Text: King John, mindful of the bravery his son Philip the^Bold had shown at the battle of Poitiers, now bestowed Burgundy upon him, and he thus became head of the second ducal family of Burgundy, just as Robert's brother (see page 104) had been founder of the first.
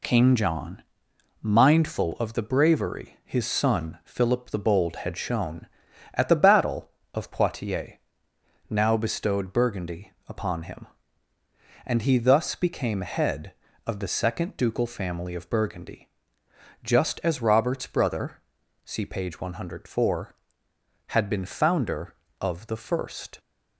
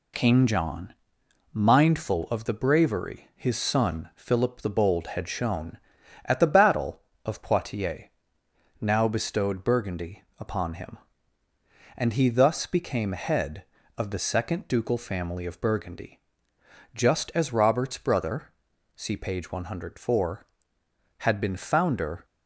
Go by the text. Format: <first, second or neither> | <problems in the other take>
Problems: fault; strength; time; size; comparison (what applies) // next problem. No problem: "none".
first | pauses between "Burgundy" and "upon"; slight; at 10.2 s; 0.16 s long; slight in the first // stops before "of the first"; at 22.2 s